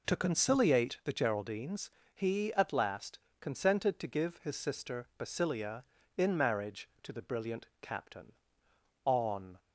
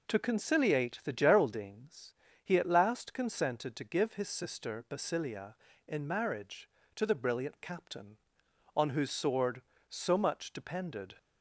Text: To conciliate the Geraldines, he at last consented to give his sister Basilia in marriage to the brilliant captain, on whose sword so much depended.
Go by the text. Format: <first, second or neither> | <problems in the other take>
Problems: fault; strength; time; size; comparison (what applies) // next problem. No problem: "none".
second | pauses between "last" and "consented"; slight; at 3.1 s; 0.22 s long // pauses between "brilliant" and "captain"; slight; at 7.6 s; 0.16 s long // stops before "whose sword so much depended"; at 9.5 s